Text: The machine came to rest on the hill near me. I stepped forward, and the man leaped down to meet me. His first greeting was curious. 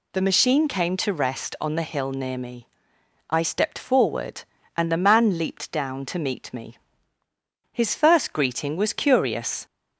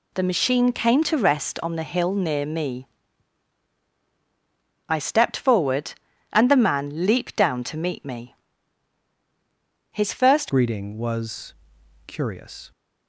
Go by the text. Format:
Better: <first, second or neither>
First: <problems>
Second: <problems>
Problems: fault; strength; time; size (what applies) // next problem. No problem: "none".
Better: first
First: none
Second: changes voice at "greeting"; from 10.4 s on; 2.3 s long // pauses between "was" and "curious"; noticeable; at 11.5 s; 0.54 s long